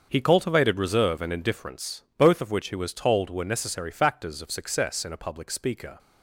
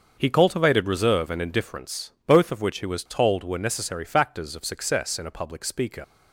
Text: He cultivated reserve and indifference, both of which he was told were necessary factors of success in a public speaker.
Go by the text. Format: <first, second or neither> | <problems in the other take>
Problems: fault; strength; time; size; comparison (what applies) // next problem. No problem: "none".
first | starts louder than the rest; until 1.1 s; 6.5 dB; also in the first // leaves "speaker" unfinished; at 6.0 s; 75 ms